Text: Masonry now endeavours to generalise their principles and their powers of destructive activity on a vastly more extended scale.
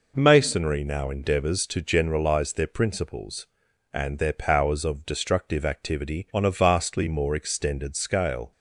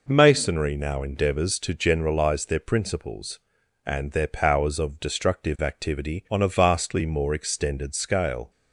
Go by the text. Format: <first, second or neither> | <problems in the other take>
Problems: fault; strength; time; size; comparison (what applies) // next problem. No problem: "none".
neither | none